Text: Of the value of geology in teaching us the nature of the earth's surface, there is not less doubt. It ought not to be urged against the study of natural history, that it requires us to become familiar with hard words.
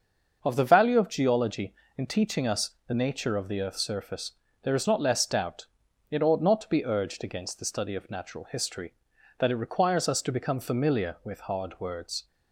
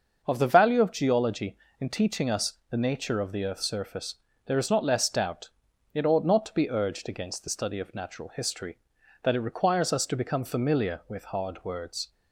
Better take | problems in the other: neither | starts louder than the rest; the same in both // pauses between "us" and "the"; slight; the same in both

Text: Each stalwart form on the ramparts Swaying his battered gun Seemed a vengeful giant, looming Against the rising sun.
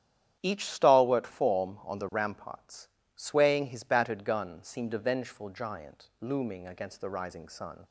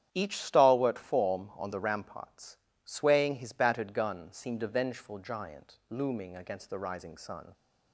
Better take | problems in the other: neither | starts louder than the rest; strong; the same in both // pauses between "ramparts" and "Swaying"; slight; the same in both

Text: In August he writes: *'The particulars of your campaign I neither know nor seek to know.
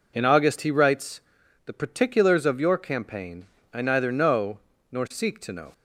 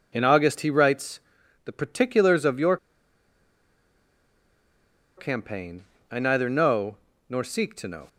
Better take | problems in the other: first | pauses between "your" and "campaign"; strong; at 2.7 s; 2.3 s long // pauses between "campaign" and "I"; slight; at 5.8 s; 0.26 s long; slight in the first // pauses between "know" and "nor"; slight; at 6.9 s; 0.32 s long; slight in the first

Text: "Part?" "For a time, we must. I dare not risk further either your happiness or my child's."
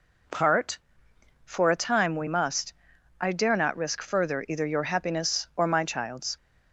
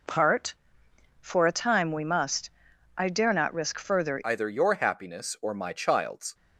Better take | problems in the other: first | changes voice at "either"; from 4.2 s on; 2.1 s long

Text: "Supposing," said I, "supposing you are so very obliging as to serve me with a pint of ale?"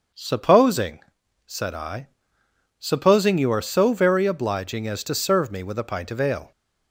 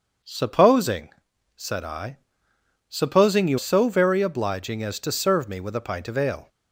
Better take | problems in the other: first | starts louder than the rest; until 1.6 s; 6.5 dB; also in the first // skips "are"; at 3.5 s

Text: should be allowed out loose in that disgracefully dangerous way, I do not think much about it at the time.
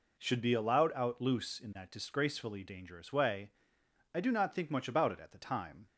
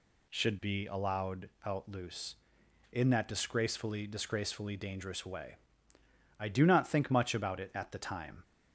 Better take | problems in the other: first | pauses between "allowed" and "out"; slight; at 1.4 s; 0.18 s long // says "disgracefully" twice; at 4.0 s

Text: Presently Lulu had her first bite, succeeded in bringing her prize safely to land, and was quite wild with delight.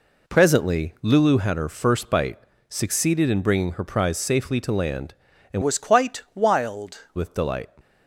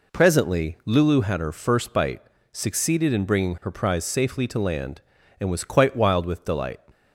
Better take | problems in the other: second | changes voice from "was" to "wild"; from 5.6 to 6.9 s; 1.3 s long

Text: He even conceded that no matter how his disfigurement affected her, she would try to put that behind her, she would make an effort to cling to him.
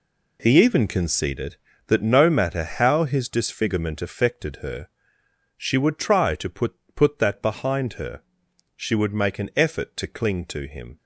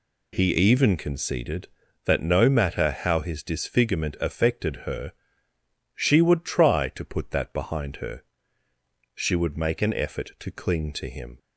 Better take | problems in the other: second | says "put" twice; at 6.9 s

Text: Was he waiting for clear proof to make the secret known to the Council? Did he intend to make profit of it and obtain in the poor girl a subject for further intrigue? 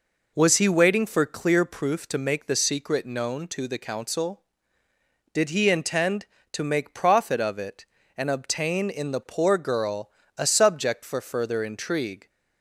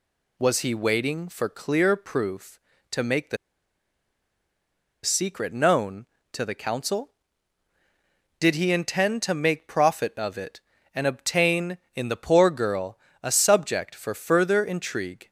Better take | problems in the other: first | pauses between "the" and "secret"; strong; at 3.3 s; 1.6 s long // pauses between "girl" and "a"; slight; at 12.9 s; 0.24 s long; slight in the first

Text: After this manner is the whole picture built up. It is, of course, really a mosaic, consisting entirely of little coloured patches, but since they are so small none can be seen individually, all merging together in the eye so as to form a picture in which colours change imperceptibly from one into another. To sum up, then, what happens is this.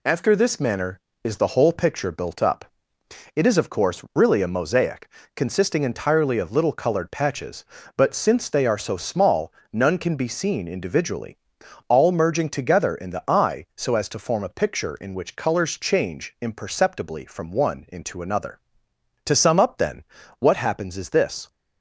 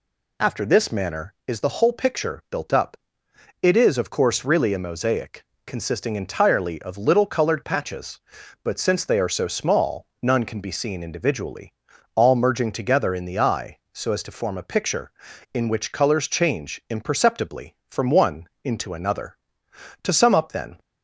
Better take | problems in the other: first | pauses between "small" and "none"; slight; at 10.0 s; 0.16 s long; slight in the first // pauses between "one" and "into"; slight; at 18.4 s; 0.16 s long // stops before "what happens is this"; at 20.7 s

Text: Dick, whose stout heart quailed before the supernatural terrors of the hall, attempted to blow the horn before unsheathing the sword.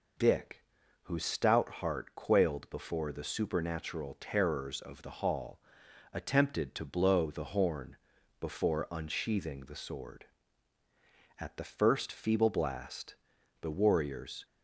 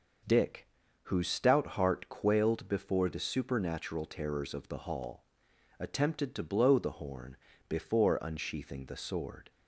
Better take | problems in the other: second | pauses between "horn" and "before"; at 7.9 s; 0.42 s long; slight in the second // goes on to say "At the first feeble blast the warriors"; strong; from 11.3 s on; 3.0 s long

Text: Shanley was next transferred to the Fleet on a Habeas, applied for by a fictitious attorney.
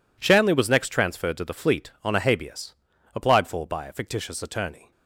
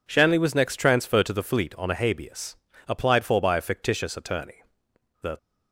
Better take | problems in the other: first | goes on to say "The"; slight; from 5.2 s on; 0.16 s long

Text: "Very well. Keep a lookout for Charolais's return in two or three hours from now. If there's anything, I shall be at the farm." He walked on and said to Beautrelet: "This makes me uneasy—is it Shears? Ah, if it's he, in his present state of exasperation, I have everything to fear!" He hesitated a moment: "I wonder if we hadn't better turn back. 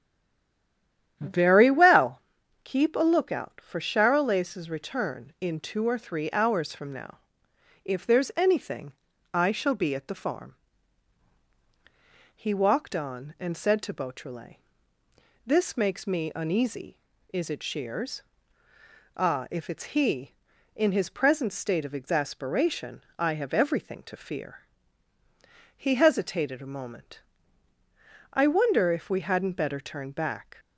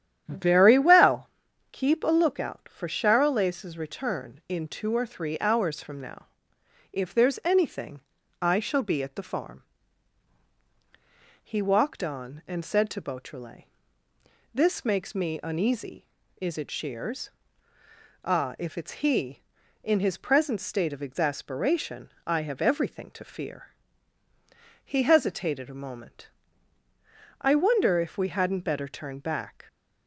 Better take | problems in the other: second | stays silent before the first word; noticeable; until 1.1 s; 1.1 s long // starts louder than the rest; strong; until 2.2 s; 10 dB; strong in the second

